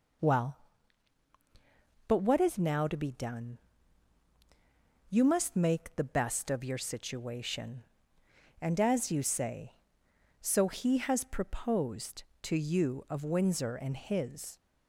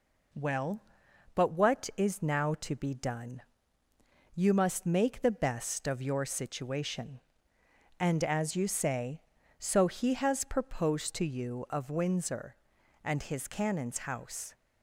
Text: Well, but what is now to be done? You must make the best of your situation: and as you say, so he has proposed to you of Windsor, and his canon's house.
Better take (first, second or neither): second